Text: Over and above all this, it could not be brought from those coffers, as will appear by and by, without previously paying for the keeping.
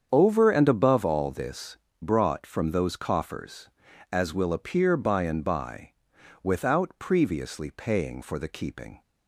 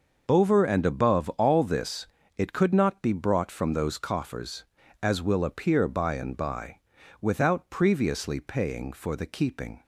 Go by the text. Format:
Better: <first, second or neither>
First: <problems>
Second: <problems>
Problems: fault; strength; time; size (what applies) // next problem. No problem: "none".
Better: second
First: starts louder than the rest; strong; until 1.1 s; 7.5 dB // skips "it could not be"; at 1.8 s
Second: none